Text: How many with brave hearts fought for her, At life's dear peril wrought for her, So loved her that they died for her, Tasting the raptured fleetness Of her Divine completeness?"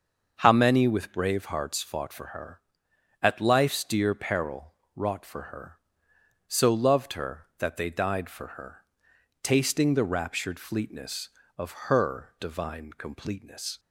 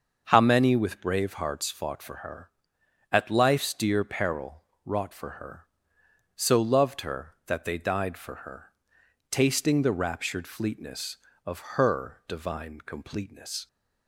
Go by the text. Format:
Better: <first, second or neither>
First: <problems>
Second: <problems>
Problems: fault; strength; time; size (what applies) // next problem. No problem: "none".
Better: neither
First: starts louder than the rest; until 1.4 s; 6.5 dB // pauses between "peril" and "wrought"; slight; at 4.7 s; 0.20 s long // pauses between "Of" and "her"; slight; at 11.7 s; 0.16 s long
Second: starts louder than the rest; until 1.2 s; 6.5 dB // pauses between "peril" and "wrought"; slight; at 4.6 s; 0.20 s long // pauses between "Of" and "her"; slight; at 11.5 s; 0.16 s long